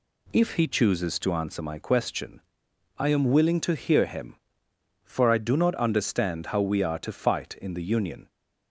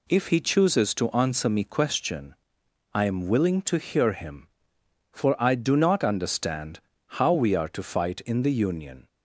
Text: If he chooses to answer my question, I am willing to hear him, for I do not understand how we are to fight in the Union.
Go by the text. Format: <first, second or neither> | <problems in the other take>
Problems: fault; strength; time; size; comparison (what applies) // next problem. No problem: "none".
first | says "me" for "my"; at 1.4 s // pauses between "understand" and "how"; at 6.7 s; 0.40 s long